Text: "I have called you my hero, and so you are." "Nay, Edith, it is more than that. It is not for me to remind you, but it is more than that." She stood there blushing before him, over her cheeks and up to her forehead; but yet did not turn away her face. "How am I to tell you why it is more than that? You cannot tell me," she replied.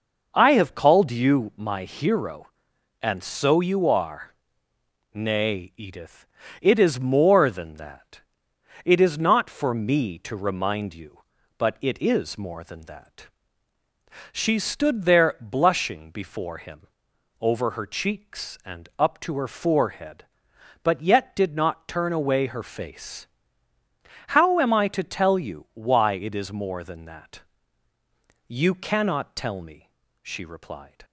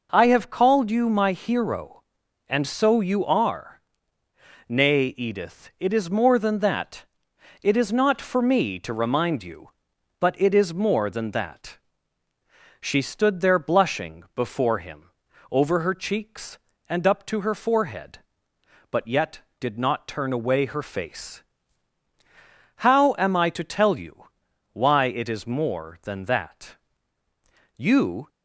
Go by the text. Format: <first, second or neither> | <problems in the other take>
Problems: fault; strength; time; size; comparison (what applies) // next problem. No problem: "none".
first | pauses between "you" and "why"; noticeable; at 24.2 s; 0.46 s long // stops before "cannot tell me she replied"; at 28.2 s